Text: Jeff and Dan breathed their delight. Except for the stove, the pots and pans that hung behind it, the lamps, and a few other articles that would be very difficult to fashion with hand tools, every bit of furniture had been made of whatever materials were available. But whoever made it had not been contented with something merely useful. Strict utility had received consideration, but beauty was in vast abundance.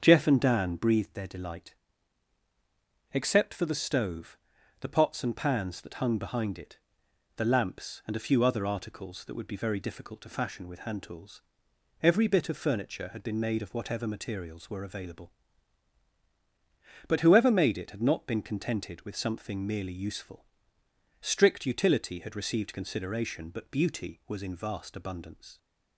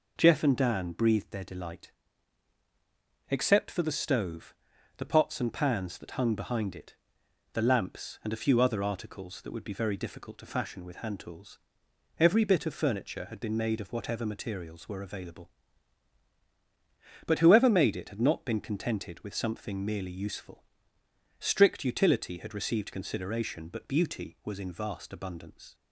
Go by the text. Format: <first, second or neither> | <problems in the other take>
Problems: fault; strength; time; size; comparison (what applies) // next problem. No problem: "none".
second | starts louder than the rest; until 0.9 s; 6.5 dB